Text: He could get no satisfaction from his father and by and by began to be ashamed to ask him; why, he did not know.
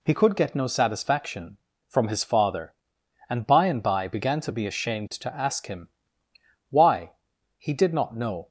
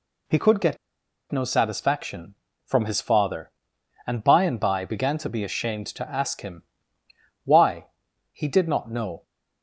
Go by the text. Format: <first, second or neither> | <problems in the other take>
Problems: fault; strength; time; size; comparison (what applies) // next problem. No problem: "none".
first | pauses between "get" and "no"; noticeable; at 0.7 s; 0.55 s long